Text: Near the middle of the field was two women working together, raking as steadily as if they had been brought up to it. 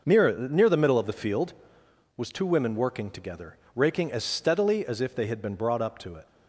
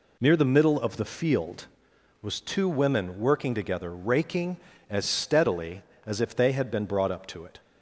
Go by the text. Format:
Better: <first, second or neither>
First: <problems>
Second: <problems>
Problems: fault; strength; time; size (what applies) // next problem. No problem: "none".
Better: second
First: says "Near" twice; at 0.3 s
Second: none